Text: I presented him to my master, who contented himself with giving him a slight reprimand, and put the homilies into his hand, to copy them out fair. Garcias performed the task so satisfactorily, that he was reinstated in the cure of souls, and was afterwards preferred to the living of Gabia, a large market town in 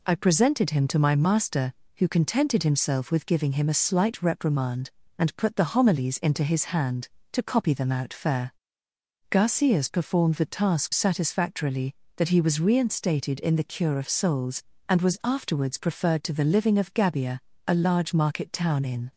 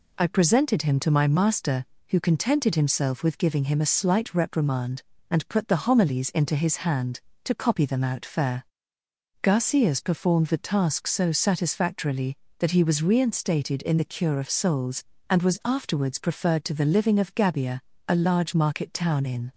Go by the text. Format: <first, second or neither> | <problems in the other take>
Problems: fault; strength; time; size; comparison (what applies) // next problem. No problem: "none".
second | skips "so"; at 10.9 s